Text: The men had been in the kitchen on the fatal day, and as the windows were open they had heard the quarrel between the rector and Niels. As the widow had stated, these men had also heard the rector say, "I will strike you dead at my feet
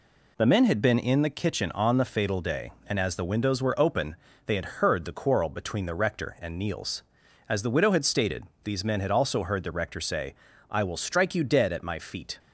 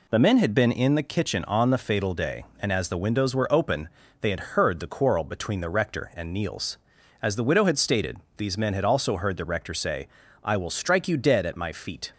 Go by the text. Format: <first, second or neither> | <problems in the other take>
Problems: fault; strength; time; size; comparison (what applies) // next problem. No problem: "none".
neither | pauses between "open" and "they"; slight; the same in both